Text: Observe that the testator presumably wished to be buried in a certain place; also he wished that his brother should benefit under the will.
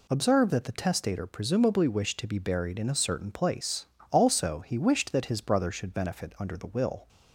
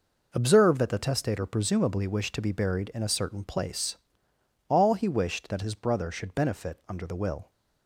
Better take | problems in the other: first | says "all" for "also"; at 4.6 s

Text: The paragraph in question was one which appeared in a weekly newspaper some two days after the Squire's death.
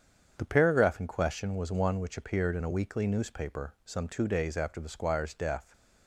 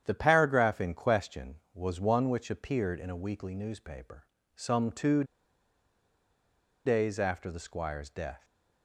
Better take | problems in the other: first | starts louder than the rest; strong; until 1.0 s; 9 dB; strong in the first // pauses between "newspaper" and "some"; slight; at 4.2 s; 0.28 s long // pauses between "two" and "days"; strong; at 5.2 s; 1.6 s long

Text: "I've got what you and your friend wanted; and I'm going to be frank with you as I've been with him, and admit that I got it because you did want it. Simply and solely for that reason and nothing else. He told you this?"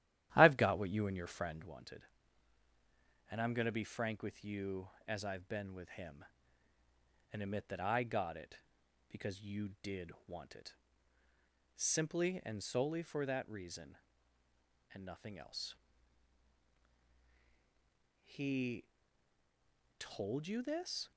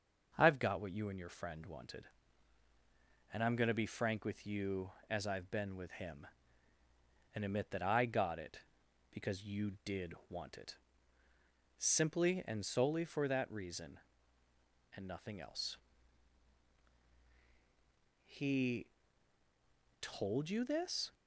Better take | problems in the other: second | starts louder than the rest; strong; until 1.7 s; 12 dB // pauses between "did" and "want"; slight; at 10.1 s; 0.16 s long; slight in the second // pauses between "He" and "told"; at 18.8 s; 1.1 s long; also in the second

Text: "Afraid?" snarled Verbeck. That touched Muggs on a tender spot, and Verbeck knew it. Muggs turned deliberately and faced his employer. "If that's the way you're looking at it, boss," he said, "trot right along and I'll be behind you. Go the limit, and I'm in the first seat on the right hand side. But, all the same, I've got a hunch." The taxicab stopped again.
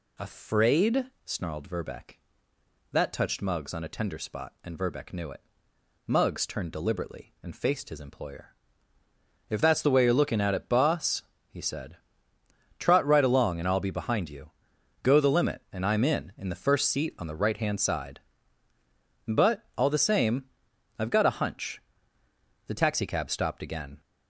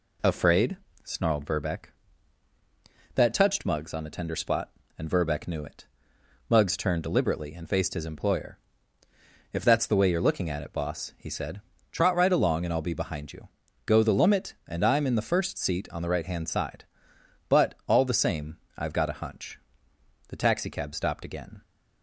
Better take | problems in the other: second | says "in" twice; at 16.3 s

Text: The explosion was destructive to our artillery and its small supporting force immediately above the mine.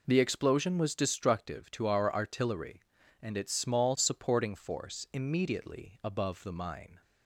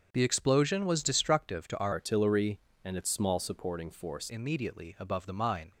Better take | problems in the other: first | starts louder than the rest; until 1.1 s; 7 dB // changes voice from "artillery" to "force"; from 1.9 to 4.3 s; 2.4 s long

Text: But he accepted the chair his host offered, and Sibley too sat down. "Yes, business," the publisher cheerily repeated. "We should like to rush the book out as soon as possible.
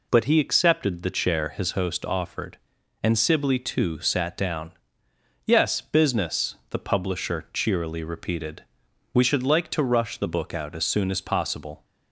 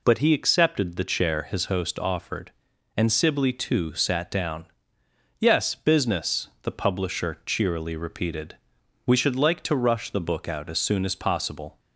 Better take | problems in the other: neither | none

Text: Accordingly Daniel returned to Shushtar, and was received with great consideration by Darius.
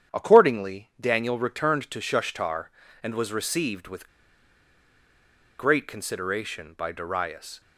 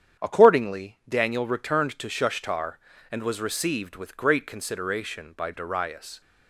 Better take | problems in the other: second | starts louder than the rest; strong; until 1.2 s; 8.5 dB; strong in the second // pauses between "with" and "great"; strong; at 4.0 s; 1.4 s long

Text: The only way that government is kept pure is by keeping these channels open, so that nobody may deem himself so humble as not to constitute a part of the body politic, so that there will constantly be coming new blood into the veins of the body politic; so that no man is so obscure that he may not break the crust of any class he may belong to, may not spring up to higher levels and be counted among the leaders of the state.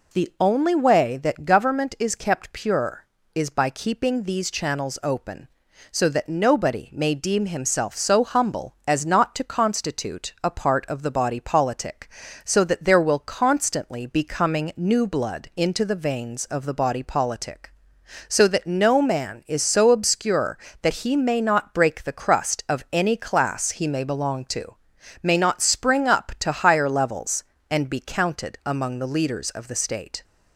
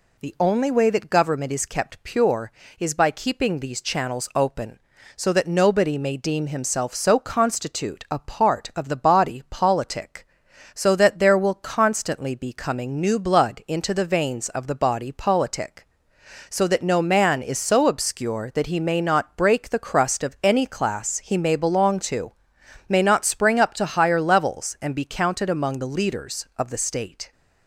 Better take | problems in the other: first | skips "humble as not to"; at 7.1 s

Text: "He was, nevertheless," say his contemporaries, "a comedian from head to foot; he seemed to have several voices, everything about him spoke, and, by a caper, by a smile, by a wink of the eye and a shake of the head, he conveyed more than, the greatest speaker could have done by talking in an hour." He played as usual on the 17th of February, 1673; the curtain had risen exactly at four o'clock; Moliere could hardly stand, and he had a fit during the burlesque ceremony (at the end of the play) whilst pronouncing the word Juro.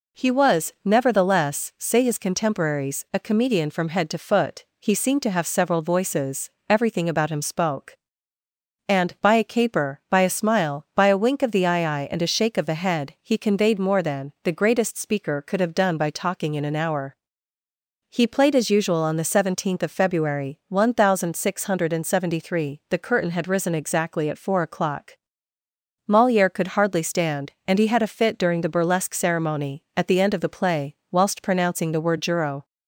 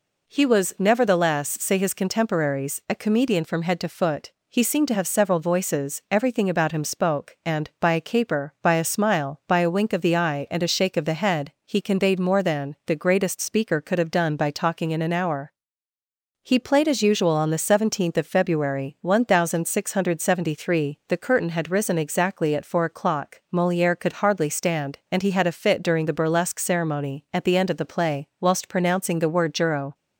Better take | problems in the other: second | says "eye" twice; at 12.0 s

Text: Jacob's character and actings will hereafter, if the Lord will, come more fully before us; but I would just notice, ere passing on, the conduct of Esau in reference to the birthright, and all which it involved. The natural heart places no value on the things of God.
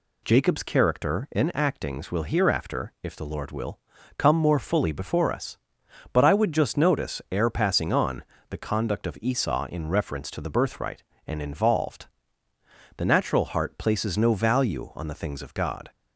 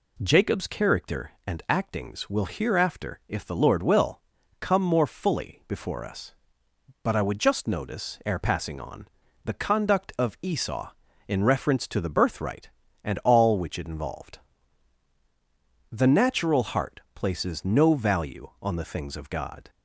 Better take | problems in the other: second | skips "all which it"; at 11.4 s

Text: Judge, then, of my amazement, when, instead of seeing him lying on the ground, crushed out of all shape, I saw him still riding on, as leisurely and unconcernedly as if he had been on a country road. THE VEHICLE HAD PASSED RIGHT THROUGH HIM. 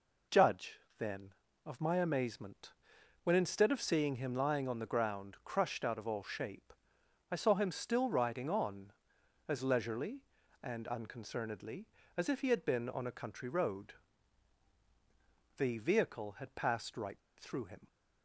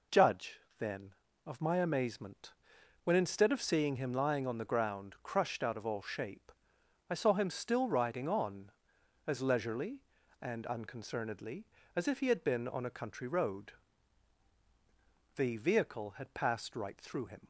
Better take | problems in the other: second | pauses between "RIGHT" and "THROUGH"; slight; at 17.1 s; 0.20 s long

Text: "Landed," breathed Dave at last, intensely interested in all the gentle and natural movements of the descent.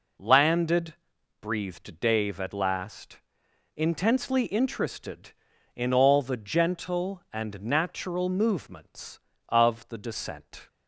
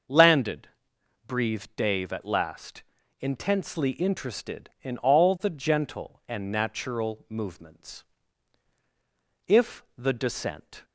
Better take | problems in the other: first | starts louder than the rest; until 1.6 s; 6.5 dB // says "if" for "of"; at 9.4 s

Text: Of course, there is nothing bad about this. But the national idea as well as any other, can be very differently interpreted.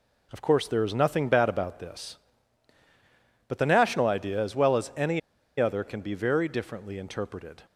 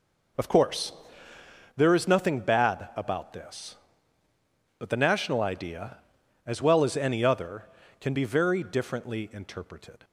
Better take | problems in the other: second | pauses between "any" and "other"; at 5.1 s; 0.40 s long

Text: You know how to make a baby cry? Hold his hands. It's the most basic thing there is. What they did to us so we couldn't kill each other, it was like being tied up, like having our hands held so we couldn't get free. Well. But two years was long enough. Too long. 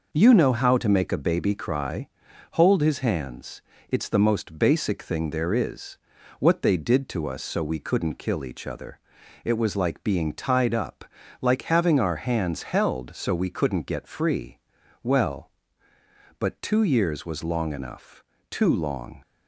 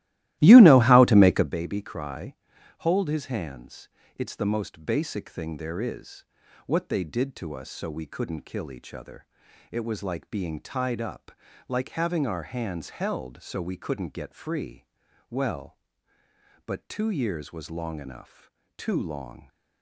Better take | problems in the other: first | starts louder than the rest; strong; until 1.5 s; 16 dB

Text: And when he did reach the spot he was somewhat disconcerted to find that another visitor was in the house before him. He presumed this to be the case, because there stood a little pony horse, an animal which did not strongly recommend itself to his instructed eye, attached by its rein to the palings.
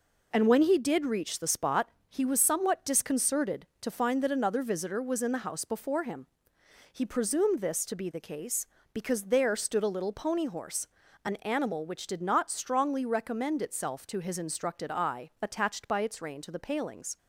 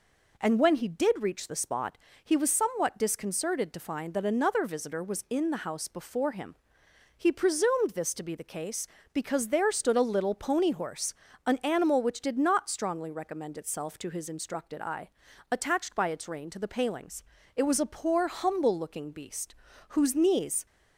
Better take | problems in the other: first | pauses between "spot" and "he"; slight; at 1.9 s; 0.26 s long; slight in the first // goes on to say "It was a poor humble looking beast whose knees"; strong; from 17.5 s on; 3.1 s long

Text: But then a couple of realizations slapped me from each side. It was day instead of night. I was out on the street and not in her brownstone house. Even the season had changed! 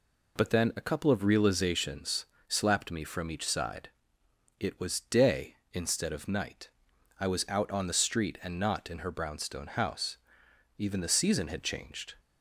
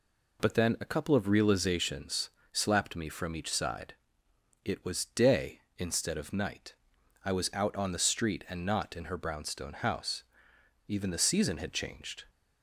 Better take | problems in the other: neither | pauses between "realizations" and "slapped"; slight; the same in both

